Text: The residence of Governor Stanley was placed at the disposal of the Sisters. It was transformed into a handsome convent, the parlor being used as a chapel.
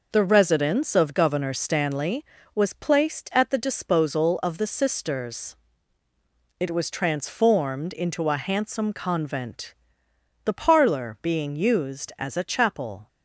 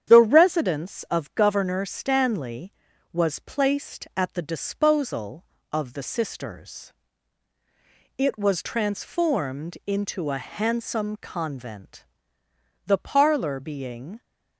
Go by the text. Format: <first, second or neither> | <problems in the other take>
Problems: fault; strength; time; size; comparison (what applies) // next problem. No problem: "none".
first | starts louder than the rest; strong; until 1.1 s; 9 dB // stops before "used as a chapel"; at 14.2 s